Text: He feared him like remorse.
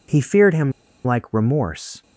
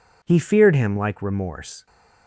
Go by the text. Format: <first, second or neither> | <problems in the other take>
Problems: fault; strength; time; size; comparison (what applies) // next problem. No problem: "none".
second | pauses between "him" and "like"; slight; at 0.7 s; 0.33 s long